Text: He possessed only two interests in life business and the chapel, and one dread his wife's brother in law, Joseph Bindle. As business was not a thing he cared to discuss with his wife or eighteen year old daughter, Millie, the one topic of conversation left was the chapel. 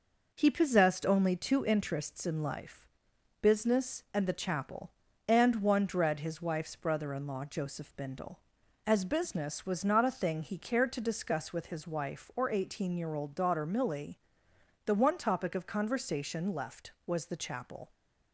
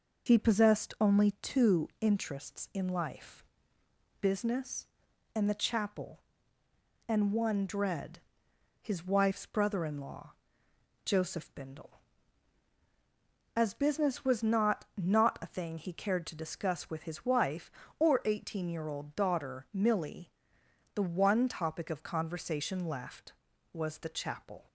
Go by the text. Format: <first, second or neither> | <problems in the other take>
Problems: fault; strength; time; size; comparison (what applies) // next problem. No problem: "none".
first | pauses between "life" and "business"; noticeable; at 3.4 s; 0.74 s long; noticeable in the first // pauses between "dread" and "his"; noticeable; at 8.1 s; 0.62 s long // says "not" twice; at 14.9 s